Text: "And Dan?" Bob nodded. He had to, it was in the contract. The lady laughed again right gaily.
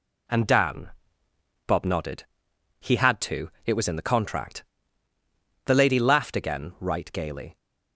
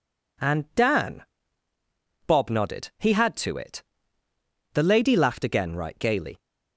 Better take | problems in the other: first | skips "was in the contract"; at 4.2 s

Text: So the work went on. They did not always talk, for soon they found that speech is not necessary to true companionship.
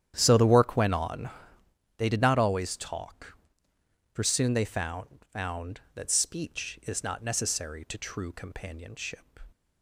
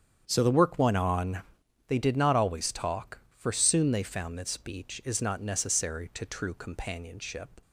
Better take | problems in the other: second | starts louder than the rest; strong; until 1.1 s; 10 dB; strong in the second // says "found" twice; at 5.3 s

